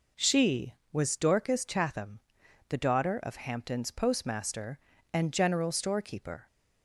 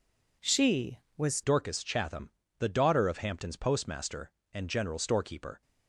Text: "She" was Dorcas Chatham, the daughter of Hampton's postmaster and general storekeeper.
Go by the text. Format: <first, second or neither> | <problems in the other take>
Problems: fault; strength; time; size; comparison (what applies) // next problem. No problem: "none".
first | changes voice at "Dorcas"; from 1.4 s on; 4.2 s long